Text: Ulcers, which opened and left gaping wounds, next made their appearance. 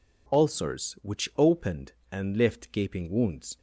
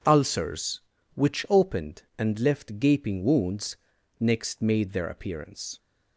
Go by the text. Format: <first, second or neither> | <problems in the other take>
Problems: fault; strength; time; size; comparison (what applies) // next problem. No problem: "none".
second | stops before "next made their appearance"; at 3.5 s